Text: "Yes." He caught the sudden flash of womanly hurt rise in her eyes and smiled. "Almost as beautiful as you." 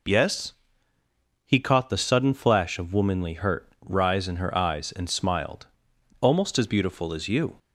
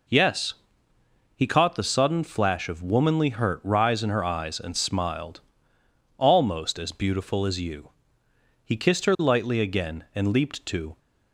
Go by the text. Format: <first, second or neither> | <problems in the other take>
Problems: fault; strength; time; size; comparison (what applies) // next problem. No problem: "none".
first | goes on to say "He kissed her lightly again and leaped to"; strong; from 8.6 s on; 2.3 s long